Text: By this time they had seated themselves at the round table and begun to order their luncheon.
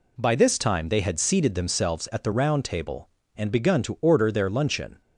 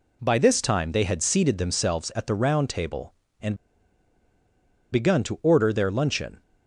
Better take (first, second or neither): first